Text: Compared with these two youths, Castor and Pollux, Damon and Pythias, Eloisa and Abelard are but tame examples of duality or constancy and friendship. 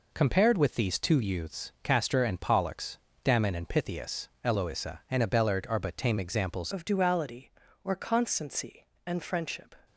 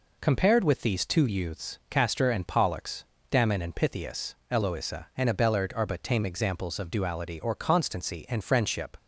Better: second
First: changes voice at "of"; from 6.7 s on; 3.0 s long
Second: none

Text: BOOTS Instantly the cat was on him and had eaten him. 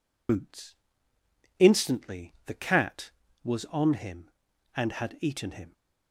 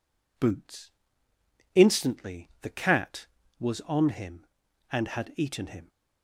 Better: second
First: loses the start of "BOOTS"; at 0.2 s; 65 ms // pauses between "BOOTS" and "Instantly"; noticeable; at 0.7 s; 0.82 s long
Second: pauses between "BOOTS" and "Instantly"; noticeable; at 0.9 s; 0.82 s long

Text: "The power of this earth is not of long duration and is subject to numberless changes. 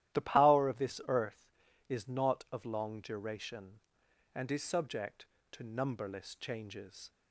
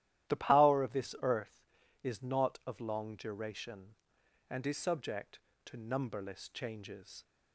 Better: neither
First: starts louder than the rest; strong; until 1.2 s; 13 dB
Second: starts louder than the rest; strong; until 1.3 s; 13 dB

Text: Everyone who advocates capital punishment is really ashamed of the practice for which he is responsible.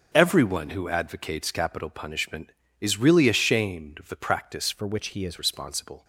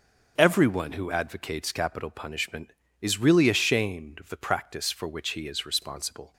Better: second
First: starts louder than the rest; until 1.1 s; 6 dB // changes voice from "for" to "is"; from 4.7 to 5.3 s; 0.6 s long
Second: starts louder than the rest; noticeable; until 1.4 s; 6 dB

